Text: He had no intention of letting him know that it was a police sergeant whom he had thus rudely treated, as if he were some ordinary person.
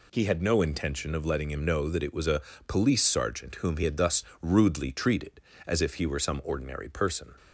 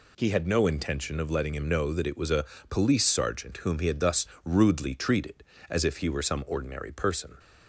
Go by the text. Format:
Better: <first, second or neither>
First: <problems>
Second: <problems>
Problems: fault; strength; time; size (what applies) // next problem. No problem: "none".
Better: neither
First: pauses between "a" and "police"; slight; at 2.4 s; 0.26 s long // pauses between "thus" and "rudely"; slight; at 4.2 s; 0.18 s long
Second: pauses between "a" and "police"; slight; at 2.4 s; 0.26 s long // pauses between "thus" and "rudely"; slight; at 4.2 s; 0.18 s long